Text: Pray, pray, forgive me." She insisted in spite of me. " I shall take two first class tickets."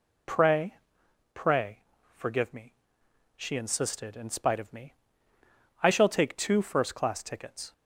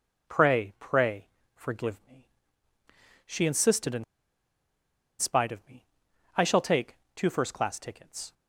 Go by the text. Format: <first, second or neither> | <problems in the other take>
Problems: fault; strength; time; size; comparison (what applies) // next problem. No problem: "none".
first | pauses between "in" and "spite"; at 4.0 s; 1.1 s long // pauses between "take" and "two"; slight; at 6.9 s; 0.18 s long